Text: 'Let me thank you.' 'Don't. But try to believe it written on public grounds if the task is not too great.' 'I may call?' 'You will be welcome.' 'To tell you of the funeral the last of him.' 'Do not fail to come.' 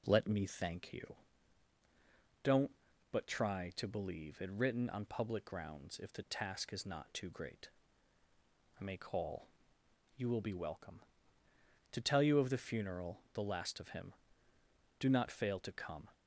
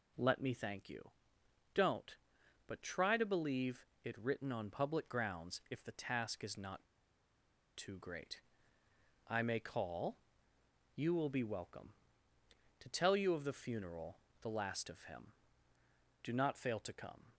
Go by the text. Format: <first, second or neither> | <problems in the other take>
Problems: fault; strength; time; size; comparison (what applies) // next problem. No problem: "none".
first | pauses between "believe" and "it"; slight; at 3.8 s; 0.18 s long // pauses between "not" and "too"; noticeable; at 6.8 s; 0.91 s long // pauses between "funeral" and "the"; slight; at 14.2 s; 0.20 s long